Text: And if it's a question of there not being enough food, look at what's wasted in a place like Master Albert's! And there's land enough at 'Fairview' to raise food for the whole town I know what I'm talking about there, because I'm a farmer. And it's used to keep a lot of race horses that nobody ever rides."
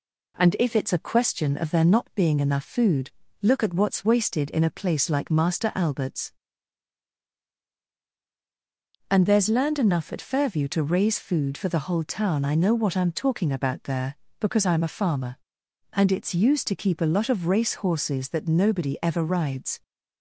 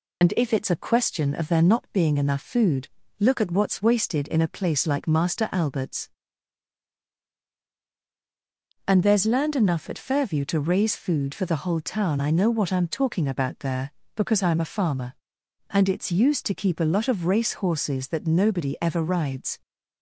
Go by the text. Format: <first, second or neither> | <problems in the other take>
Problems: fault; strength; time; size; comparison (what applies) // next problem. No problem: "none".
first | loses the start of "And"; at 0.2 s; 75 ms